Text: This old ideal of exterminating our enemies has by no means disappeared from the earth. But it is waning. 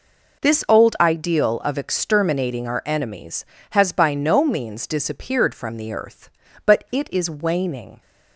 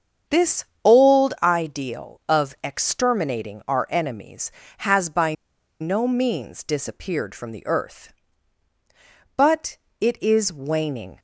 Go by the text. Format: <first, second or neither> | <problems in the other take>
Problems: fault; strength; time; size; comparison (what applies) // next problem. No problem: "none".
first | starts louder than the rest; strong; until 1.5 s; 7.5 dB // pauses between "This" and "old"; slight; at 0.6 s; 0.18 s long // pauses between "by" and "no"; noticeable; at 5.3 s; 0.47 s long // pauses between "But" and "it"; slight; at 9.7 s; 0.24 s long